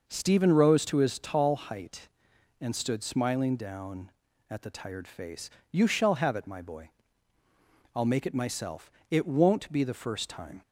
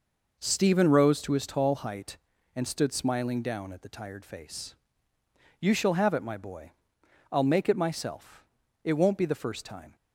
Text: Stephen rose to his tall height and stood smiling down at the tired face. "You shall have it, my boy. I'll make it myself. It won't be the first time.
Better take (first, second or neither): neither